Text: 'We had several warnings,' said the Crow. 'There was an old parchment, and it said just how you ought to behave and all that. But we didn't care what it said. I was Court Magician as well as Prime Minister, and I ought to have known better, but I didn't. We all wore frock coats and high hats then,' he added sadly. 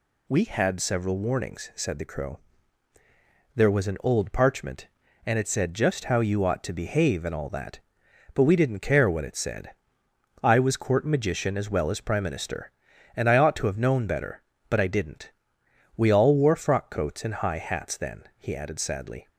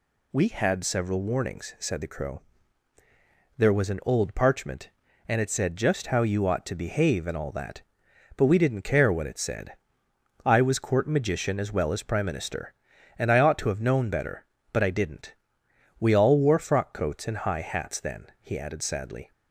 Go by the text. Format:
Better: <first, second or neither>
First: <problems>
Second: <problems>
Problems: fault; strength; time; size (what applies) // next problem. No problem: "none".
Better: neither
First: none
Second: none